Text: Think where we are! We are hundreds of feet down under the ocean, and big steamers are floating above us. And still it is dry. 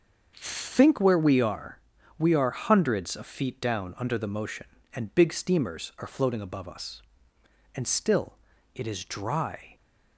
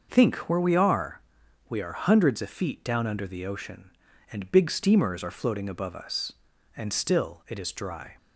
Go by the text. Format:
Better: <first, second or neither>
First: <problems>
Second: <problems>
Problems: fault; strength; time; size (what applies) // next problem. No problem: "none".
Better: second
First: starts louder than the rest; until 1.3 s; 6 dB // says "motion" for "ocean"; at 4.2 s // pauses between "still" and "it"; at 8.3 s; 0.38 s long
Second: starts louder than the rest; noticeable; until 1.2 s; 6 dB